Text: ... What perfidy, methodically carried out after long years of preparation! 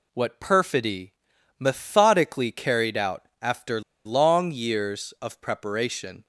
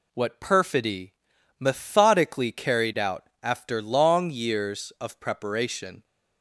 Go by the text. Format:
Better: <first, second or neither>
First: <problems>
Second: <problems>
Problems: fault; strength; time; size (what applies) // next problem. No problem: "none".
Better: second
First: pauses between "after" and "long"; slight; at 3.8 s; 0.24 s long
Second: none